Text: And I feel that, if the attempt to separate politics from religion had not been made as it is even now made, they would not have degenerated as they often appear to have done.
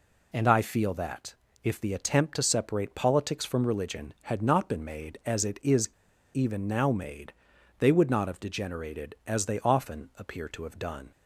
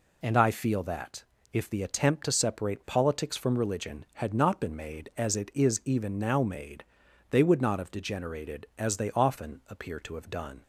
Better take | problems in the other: second | pauses between "is" and "even"; at 5.8 s; 0.44 s long

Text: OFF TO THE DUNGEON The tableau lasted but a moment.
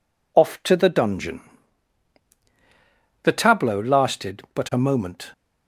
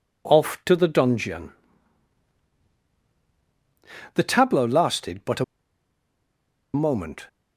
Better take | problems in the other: first | pauses between "DUNGEON" and "The"; strong; at 1.5 s; 2.6 s long; strong in the first // pauses between "a" and "moment"; strong; at 5.4 s; 1.2 s long

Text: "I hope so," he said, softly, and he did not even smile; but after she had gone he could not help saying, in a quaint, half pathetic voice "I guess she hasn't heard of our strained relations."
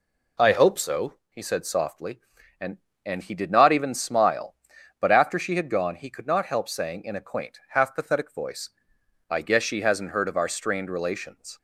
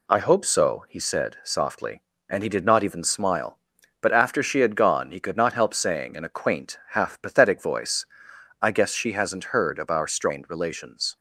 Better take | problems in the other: second | says "and" twice; at 3.0 s // pauses between "voice" and "I"; noticeable; at 8.6 s; 0.58 s long; noticeable in the second

